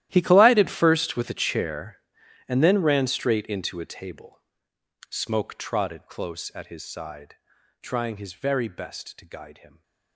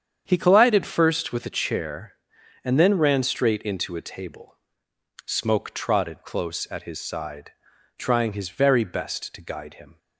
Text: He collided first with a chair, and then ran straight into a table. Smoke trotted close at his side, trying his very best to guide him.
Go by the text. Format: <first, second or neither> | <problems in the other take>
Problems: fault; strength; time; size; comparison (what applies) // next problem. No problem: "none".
second | gets quieter; strong; throughout; 19 dB // starts louder than the rest; strong; until 1.1 s; 13.5 dB; strong in the second